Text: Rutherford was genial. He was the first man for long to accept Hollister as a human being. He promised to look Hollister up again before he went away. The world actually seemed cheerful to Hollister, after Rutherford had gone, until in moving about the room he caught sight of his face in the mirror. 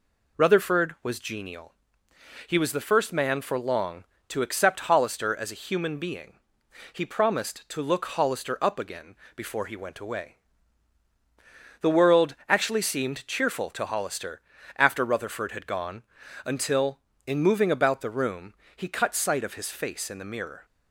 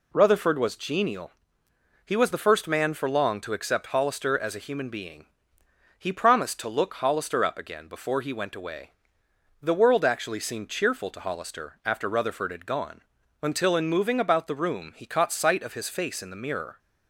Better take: second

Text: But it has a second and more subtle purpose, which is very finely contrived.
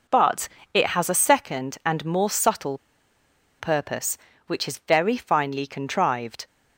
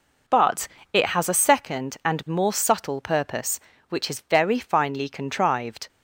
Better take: second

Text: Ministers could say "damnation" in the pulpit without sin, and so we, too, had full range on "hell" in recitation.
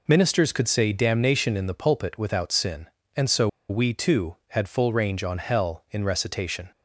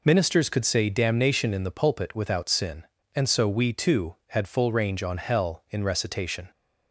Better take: second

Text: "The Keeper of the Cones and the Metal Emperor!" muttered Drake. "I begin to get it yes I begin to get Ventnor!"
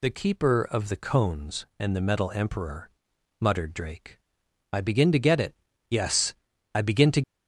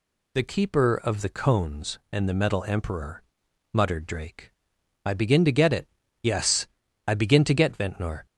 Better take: second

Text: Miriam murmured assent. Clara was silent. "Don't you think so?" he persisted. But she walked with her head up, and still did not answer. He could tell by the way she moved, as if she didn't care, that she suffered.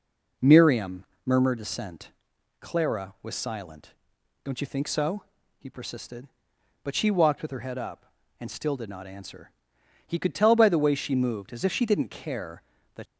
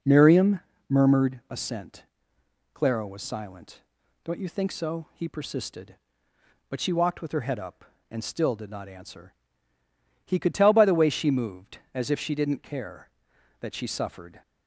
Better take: second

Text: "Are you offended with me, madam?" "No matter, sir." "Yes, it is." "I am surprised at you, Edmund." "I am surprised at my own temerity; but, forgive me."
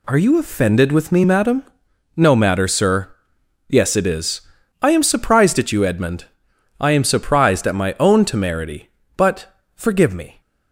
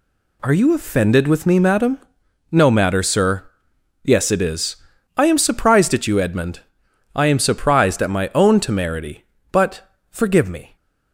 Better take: neither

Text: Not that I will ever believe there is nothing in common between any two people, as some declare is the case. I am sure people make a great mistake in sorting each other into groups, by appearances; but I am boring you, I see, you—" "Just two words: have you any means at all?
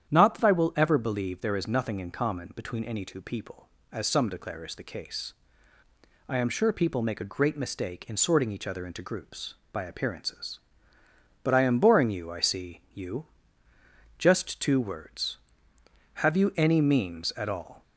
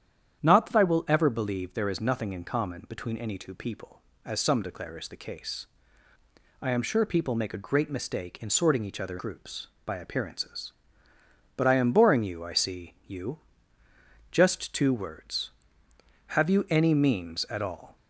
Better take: first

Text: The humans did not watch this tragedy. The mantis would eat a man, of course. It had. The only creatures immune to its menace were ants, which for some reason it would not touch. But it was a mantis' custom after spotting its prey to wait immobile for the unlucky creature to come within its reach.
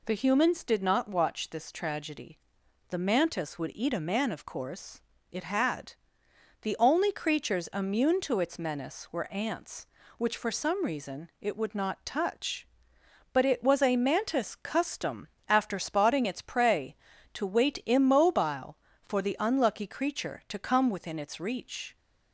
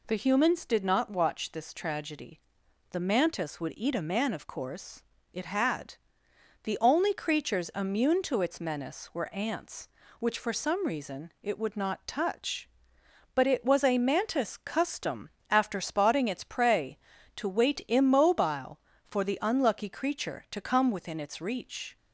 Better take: neither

